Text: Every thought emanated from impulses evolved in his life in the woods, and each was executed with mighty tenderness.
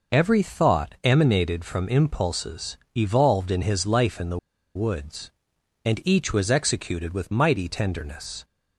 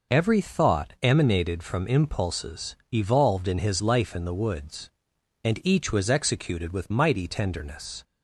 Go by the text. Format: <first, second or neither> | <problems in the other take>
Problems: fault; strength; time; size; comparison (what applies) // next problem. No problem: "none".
second | pauses between "impulses" and "evolved"; slight; at 2.7 s; 0.18 s long; slight in the second // pauses between "the" and "woods"; at 4.3 s; 0.37 s long